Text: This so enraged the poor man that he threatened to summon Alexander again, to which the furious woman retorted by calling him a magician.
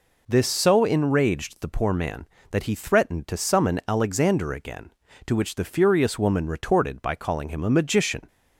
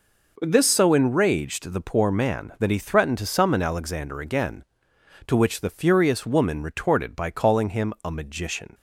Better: neither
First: none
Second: none

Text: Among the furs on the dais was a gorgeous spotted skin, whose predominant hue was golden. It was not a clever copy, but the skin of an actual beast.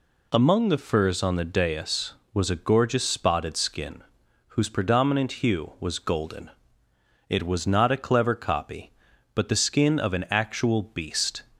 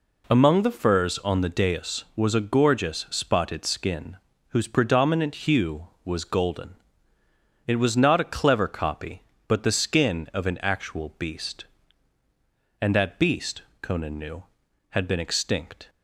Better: first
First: none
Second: goes on to say "And that beast Conan knew had been extinct"; strong; from 12.8 s on; 3.0 s long

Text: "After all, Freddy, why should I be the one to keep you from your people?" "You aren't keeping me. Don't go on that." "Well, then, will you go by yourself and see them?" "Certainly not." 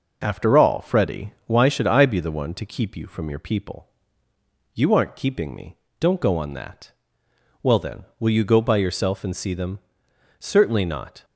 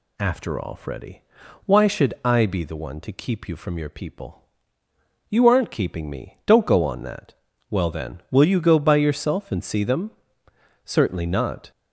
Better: neither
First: none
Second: none

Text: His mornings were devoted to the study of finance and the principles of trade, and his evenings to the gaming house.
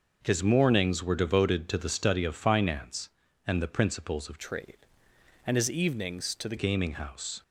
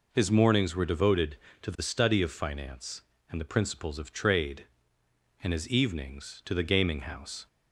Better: second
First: starts louder than the rest; noticeable; until 1.2 s; 6 dB // changes voice from "trade" to "the"; from 4.3 to 6.5 s; 2.2 s long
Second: none

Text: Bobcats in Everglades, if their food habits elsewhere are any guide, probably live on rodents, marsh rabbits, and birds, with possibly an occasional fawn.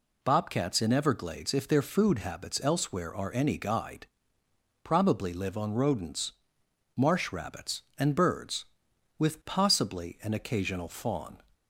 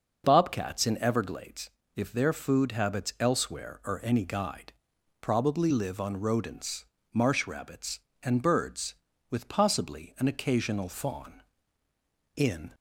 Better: first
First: none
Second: starts louder than the rest; noticeable; until 1.2 s; 6 dB // goes on to say "In"; slight; from 12.3 s on; 0.38 s long

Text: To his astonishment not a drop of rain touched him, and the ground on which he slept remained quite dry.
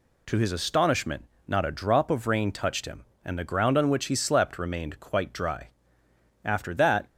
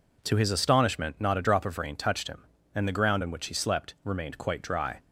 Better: second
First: pauses between "astonishment" and "not"; slight; at 1.2 s; 0.24 s long // goes on to say "After that"; noticeable; from 6.4 s on; 0.64 s long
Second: none

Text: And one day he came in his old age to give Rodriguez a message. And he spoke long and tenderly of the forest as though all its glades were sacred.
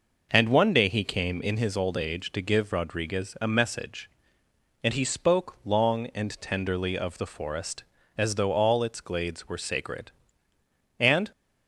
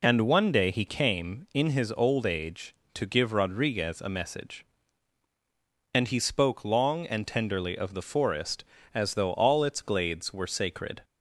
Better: second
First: goes on to say "And"; slight; from 10.9 s on; 0.32 s long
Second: none

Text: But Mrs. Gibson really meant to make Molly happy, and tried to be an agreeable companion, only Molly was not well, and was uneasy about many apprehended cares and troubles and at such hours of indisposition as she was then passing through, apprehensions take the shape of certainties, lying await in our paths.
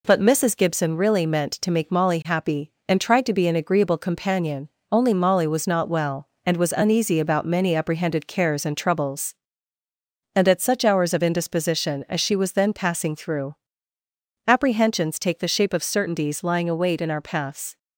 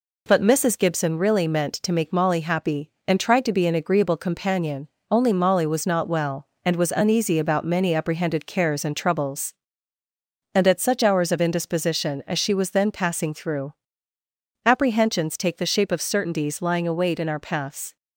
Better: neither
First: none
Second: none

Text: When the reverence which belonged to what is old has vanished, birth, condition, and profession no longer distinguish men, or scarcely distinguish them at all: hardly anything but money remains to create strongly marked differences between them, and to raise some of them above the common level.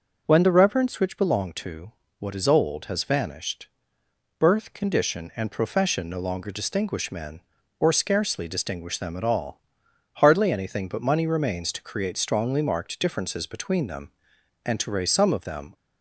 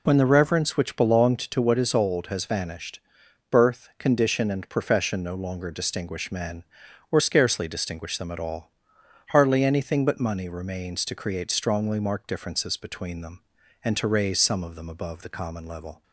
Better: second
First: pauses between "to" and "what"; slight; at 1.9 s; 0.26 s long // stops before "above the common level"; at 15.7 s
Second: none

